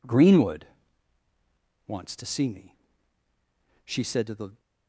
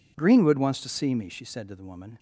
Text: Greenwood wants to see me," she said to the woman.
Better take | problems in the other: second | pauses between "Greenwood" and "wants"; at 0.6 s; 1.2 s long // stops before "woman"; at 4.5 s

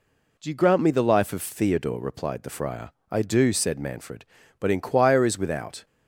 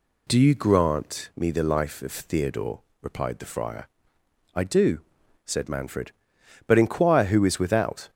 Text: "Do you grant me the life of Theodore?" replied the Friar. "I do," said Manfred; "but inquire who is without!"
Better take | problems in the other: second | skips "who"; at 5.2 s

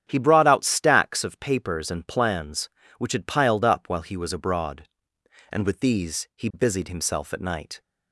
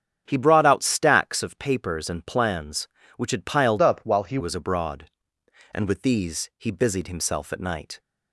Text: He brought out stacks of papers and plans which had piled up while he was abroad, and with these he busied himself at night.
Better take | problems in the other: first | starts louder than the rest; strong; until 1.2 s; 8 dB; strong in the first // changes voice from "up" to "he"; from 3.8 to 4.3 s; 0.5 s long

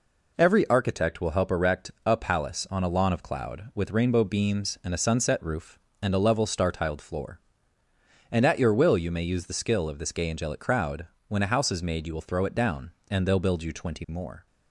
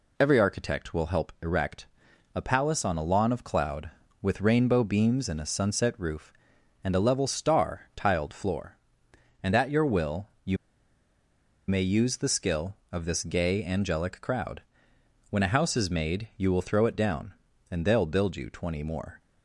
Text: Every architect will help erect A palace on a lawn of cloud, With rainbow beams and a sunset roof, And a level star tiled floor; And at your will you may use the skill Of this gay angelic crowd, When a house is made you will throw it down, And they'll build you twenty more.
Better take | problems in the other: first | pauses between "erect" and "A"; noticeable; at 1.8 s; 0.46 s long // pauses between "will" and "you"; slight; at 10.2 s; 0.16 s long // pauses between "you" and "may"; at 10.5 s; 1.1 s long

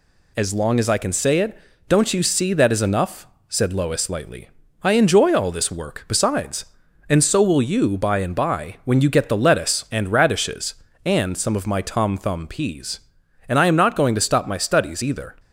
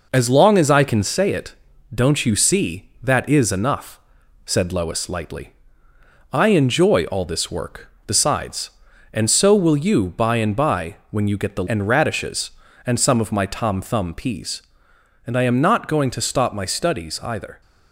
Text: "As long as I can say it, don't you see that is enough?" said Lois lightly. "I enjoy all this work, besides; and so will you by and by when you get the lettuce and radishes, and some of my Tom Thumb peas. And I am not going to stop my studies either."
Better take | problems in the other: first | skips "lettuce"; at 11.6 s

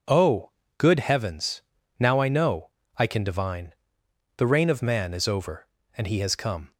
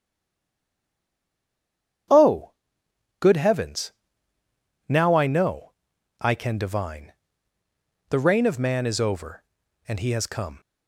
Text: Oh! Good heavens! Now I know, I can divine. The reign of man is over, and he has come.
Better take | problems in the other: first | stays silent before the first word; noticeable; until 2.0 s; 2.0 s long

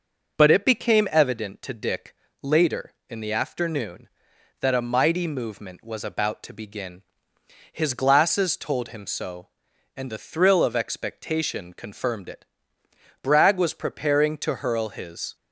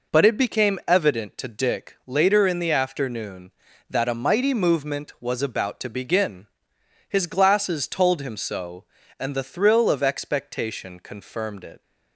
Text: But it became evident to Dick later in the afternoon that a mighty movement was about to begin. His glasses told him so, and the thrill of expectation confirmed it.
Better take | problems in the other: second | pauses between "Dick" and "later"; slight; at 2.1 s; 0.28 s long // goes on to say "Bragg was preparing to hurl his"; strong; from 13.2 s on; 2.1 s long

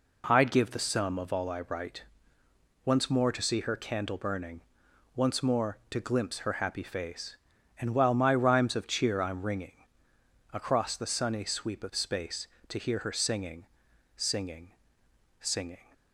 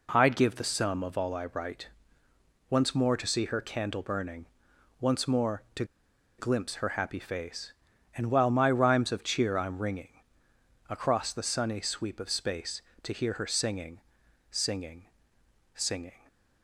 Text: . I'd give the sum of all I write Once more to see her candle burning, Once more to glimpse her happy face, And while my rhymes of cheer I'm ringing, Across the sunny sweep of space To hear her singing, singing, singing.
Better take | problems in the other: first | pauses between "write" and "Once"; noticeable; at 1.8 s; 0.80 s long; noticeable in the first // pauses between "to" and "glimpse"; noticeable; at 5.8 s; 0.54 s long

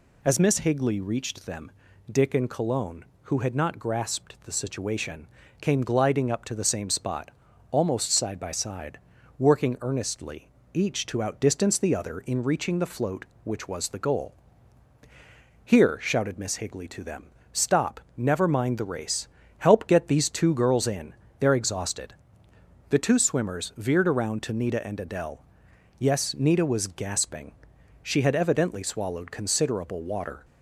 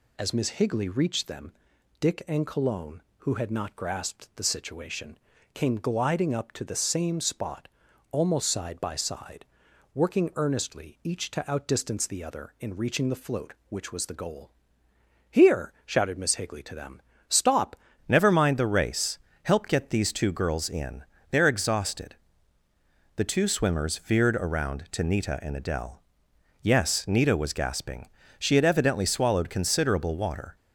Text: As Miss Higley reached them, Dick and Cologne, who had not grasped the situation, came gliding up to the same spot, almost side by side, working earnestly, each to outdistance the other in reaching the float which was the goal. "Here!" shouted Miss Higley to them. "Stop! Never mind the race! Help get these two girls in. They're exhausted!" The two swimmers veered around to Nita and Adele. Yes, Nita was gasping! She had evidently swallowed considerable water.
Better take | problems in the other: first | changes voice at "Never"; from 18.0 s on; 12.5 s long

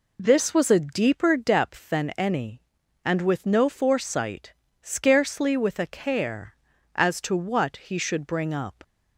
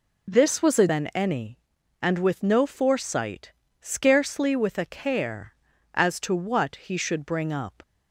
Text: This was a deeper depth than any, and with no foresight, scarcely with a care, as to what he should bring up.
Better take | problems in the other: first | skips "deeper depth"; at 0.8 s

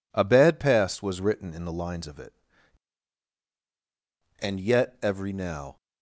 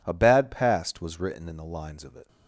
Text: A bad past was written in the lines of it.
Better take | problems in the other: second | goes on to say "And yet every now"; from 4.4 s on; 1.3 s long

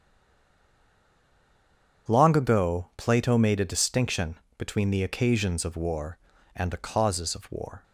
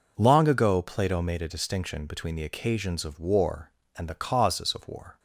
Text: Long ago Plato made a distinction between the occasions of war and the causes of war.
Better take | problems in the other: second | stays silent before the first word; noticeable; until 2.0 s; 2.0 s long // starts louder than the rest; strong; until 3.1 s; 8 dB // pauses between "distinction" and "between"; slight; at 4.3 s; 0.22 s long

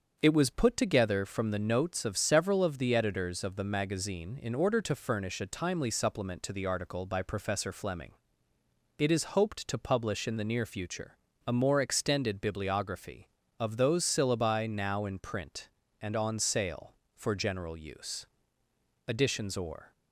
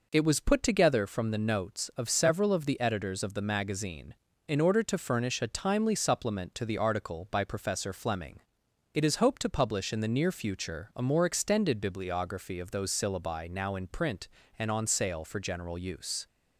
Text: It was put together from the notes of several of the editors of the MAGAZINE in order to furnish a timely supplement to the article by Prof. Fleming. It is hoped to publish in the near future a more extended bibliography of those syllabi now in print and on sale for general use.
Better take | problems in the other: second | starts louder than the rest; until 1.2 s; 7 dB // pauses between "future" and "a"; slight; at 11.1 s; 0.28 s long // goes on to say "Additions or"; noticeable; from 19.0 s on; 0.86 s long

